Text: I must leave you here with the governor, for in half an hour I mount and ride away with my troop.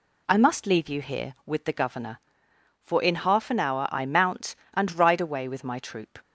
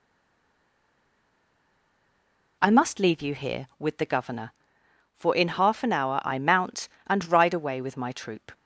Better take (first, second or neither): first